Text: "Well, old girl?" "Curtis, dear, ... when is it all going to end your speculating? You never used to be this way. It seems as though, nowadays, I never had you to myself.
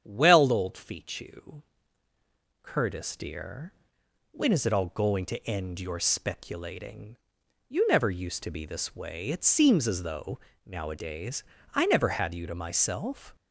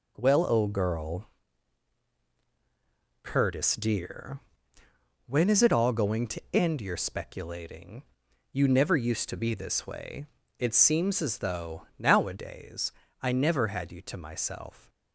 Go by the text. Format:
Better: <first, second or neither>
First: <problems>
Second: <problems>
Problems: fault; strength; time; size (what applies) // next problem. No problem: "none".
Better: second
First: starts louder than the rest; strong; until 1.0 s; 8.5 dB // says "fichu" for "girl"; at 0.7 s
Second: none